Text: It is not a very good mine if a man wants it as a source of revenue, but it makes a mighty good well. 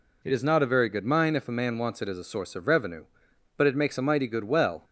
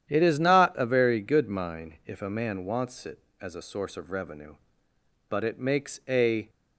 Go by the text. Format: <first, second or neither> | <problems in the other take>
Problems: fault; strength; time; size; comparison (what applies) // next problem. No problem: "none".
first | starts louder than the rest; strong; until 1.1 s; 10 dB // stops before "mighty good well"; at 6.4 s